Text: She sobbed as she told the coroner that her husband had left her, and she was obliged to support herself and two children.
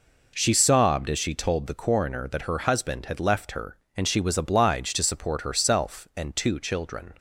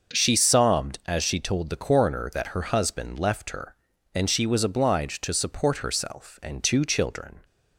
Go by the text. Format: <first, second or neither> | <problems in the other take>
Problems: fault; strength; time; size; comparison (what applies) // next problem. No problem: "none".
first | starts louder than the rest; noticeable; until 1.2 s; 6 dB // skips "had"; at 3.1 s